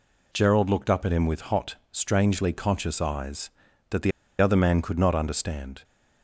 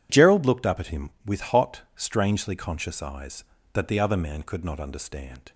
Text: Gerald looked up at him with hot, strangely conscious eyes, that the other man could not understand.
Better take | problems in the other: second | pauses between "the" and "other"; slight; at 4.1 s; 0.30 s long

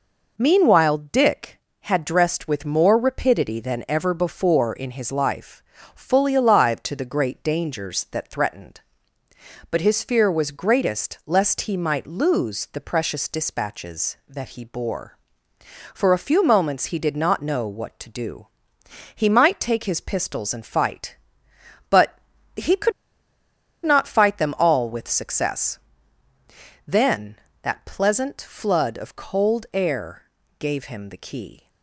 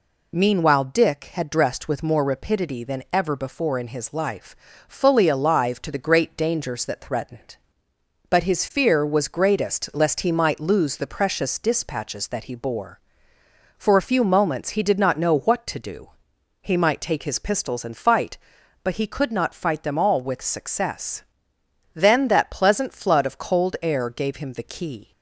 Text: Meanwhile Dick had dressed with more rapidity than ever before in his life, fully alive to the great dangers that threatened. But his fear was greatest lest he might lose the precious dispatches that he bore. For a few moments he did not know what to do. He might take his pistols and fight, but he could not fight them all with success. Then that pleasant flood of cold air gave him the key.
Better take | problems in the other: second | pauses between "but" and "he"; slight; at 22.1 s; 0.36 s long // pauses between "could" and "not"; noticeable; at 22.9 s; 0.93 s long // pauses between "air" and "gave"; at 30.2 s; 0.38 s long

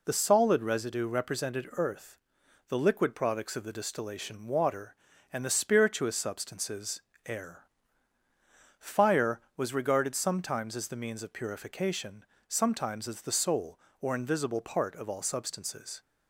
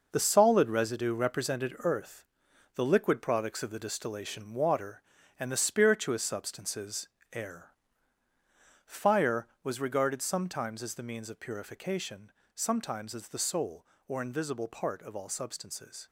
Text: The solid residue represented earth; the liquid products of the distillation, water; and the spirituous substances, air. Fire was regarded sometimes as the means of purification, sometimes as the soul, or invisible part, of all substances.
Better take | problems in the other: first | gets quieter; strong; throughout; 9 dB

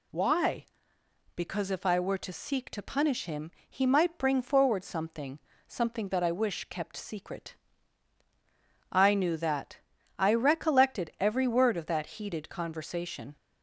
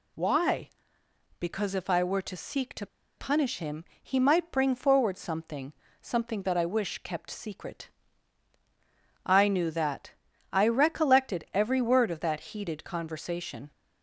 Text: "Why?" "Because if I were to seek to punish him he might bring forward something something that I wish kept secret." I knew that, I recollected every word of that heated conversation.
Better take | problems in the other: first | pauses between "to" and "punish"; slight; at 2.8 s; 0.32 s long // pauses between "him" and "he"; slight; at 3.8 s; 0.18 s long; slight in the first // pauses between "something" and "something"; slight; at 5.7 s; 0.30 s long; slight in the first

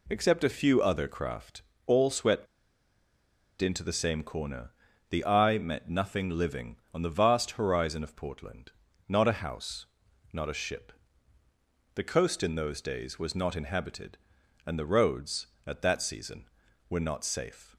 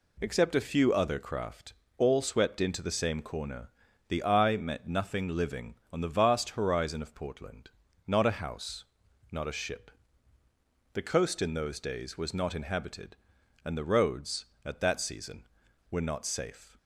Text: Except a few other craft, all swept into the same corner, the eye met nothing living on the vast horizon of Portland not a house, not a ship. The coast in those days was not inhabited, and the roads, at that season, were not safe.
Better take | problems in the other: second | pauses between "swept" and "into"; at 2.4 s; 1.1 s long // pauses between "Portland" and "not"; slight; at 8.7 s; 0.34 s long; slight in the second

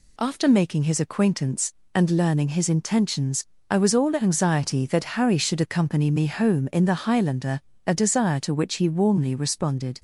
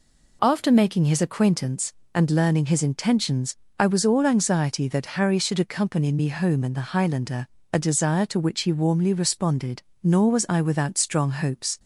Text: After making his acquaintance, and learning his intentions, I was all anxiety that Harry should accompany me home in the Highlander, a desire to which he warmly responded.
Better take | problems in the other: first | goes on to say "Nor was I without strong hopes"; strong; from 10.0 s on; 1.7 s long

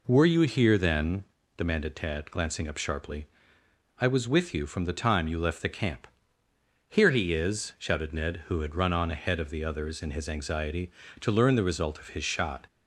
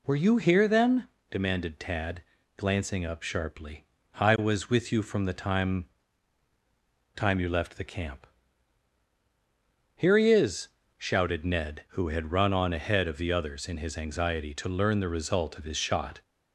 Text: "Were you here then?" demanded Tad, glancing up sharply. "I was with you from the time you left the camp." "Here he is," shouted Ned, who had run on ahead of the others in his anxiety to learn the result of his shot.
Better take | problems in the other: first | says "time" twice; at 7.1 s

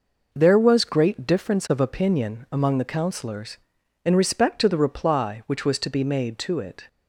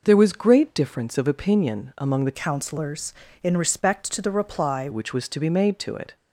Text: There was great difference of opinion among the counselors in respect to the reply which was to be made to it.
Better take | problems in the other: first | changes voice from "counselors" to "reply"; from 2.3 to 4.8 s; 2.5 s long

